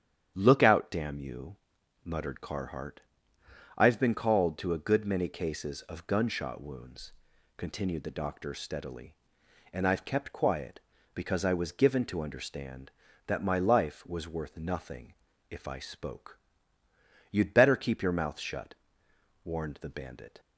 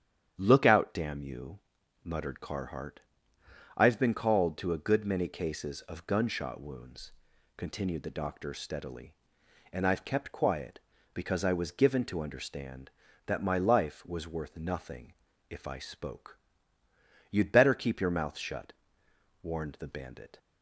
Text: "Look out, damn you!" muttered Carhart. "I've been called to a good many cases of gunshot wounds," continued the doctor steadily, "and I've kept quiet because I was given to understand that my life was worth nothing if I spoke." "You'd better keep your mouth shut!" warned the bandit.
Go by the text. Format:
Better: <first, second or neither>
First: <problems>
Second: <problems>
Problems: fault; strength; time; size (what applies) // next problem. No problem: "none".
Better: neither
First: starts louder than the rest; strong; until 1.3 s; 9 dB // pauses between "nothing" and "if"; at 15.1 s; 0.38 s long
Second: starts louder than the rest; strong; until 1.4 s; 9 dB // pauses between "nothing" and "if"; at 15.1 s; 0.38 s long